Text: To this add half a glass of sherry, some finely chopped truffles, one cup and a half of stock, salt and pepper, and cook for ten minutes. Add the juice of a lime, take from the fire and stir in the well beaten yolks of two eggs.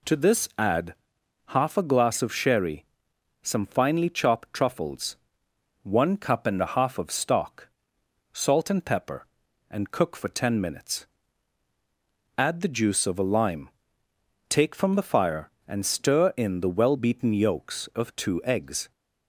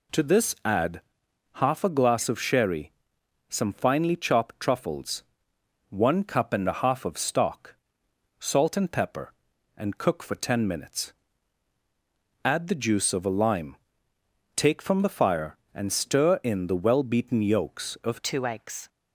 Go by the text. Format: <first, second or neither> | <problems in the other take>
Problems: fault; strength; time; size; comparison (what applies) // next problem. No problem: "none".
first | pauses between "add" and "half"; noticeable; at 1.0 s; 0.52 s long; noticeable in the first // changes voice at "two"; from 18.2 s on; 0.6 s long